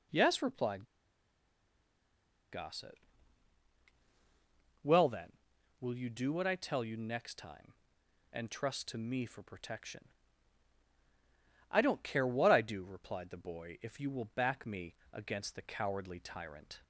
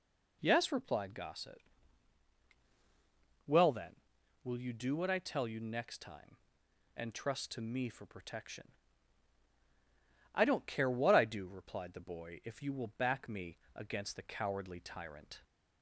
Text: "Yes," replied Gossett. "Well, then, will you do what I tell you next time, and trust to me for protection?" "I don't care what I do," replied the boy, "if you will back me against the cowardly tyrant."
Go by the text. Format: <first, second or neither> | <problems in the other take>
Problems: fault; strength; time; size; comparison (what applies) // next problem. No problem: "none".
second | pauses between "replied" and "Gossett"; strong; at 0.8 s; 1.6 s long // pauses between "me" and "against"; slight; at 14.9 s; 0.18 s long; slight in the second